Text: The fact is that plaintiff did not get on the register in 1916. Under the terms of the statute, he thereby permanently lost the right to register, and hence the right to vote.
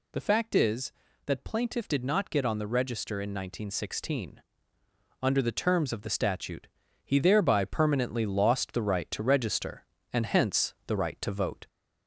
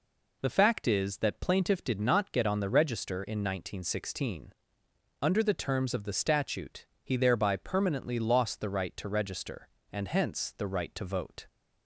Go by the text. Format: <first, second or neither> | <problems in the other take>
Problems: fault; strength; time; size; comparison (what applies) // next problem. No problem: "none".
second | gets louder; slight; throughout; 3 dB